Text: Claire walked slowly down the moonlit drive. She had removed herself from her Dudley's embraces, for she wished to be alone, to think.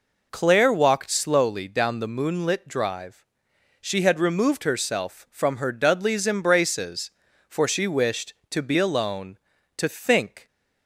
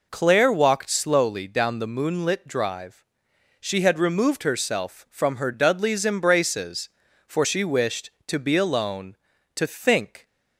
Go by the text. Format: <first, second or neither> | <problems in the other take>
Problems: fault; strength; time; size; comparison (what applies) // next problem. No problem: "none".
neither | none